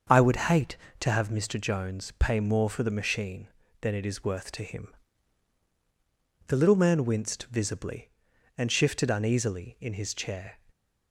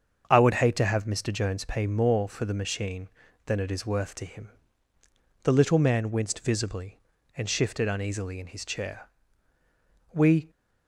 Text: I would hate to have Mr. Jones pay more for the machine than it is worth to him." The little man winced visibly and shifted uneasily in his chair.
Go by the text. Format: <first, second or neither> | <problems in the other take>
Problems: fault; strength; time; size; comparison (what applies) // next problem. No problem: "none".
first | starts louder than the rest; until 1.3 s; 7 dB; also in the first // goes on to say "We"; slight; from 10.1 s on; 0.38 s long